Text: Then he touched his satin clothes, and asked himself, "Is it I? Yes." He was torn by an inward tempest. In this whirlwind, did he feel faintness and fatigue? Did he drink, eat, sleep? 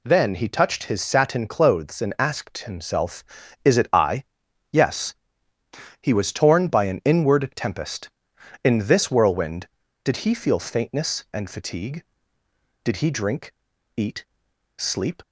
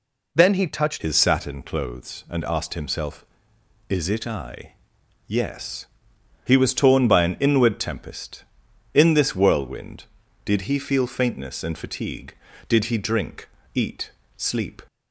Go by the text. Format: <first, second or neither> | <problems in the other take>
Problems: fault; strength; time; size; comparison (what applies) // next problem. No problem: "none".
first | changes voice at "his"; from 0.9 s on; 13.9 s long